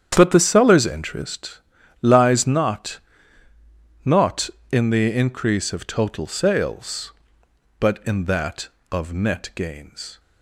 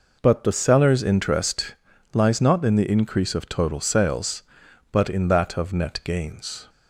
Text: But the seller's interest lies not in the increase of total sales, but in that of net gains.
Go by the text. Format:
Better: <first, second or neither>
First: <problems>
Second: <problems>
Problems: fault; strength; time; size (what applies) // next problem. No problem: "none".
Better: second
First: starts louder than the rest; strong; until 1.1 s; 9 dB // pauses between "interest" and "lies"; at 1.5 s; 0.44 s long // says "not" twice; at 4.0 s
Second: pauses between "interest" and "lies"; at 1.7 s; 0.38 s long